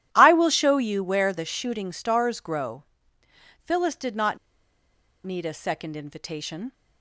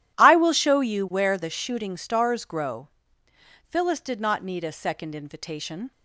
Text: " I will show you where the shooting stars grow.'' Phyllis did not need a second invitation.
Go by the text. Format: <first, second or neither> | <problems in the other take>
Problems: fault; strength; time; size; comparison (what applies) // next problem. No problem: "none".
second | pauses between "not" and "need"; noticeable; at 4.3 s; 0.88 s long